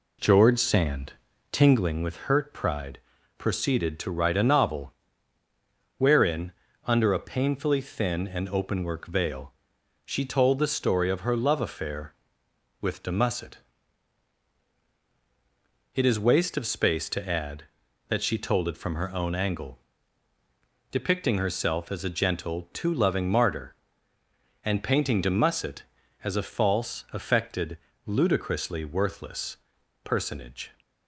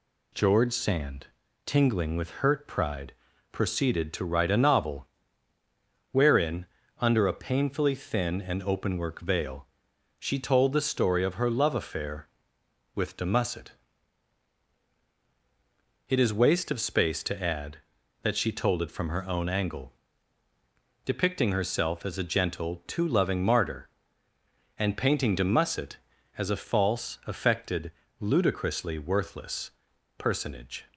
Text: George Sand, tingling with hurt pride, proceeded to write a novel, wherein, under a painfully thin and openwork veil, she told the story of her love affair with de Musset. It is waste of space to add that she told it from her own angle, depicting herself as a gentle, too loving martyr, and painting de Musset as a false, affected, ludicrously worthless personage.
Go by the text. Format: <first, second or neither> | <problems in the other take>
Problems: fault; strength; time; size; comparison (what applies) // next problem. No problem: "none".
second | starts louder than the rest; slight; until 2.0 s; 2.5 dB // pauses between "worthless" and "personage"; noticeable; at 29.5 s; 0.46 s long; noticeable in the second